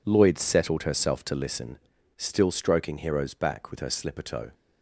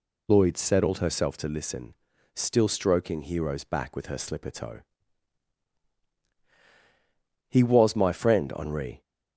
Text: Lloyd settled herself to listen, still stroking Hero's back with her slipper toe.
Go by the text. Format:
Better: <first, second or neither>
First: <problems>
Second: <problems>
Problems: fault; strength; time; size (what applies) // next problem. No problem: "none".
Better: first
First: none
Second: goes on to say "He was my friend Henri"; from 7.4 s on; 1.5 s long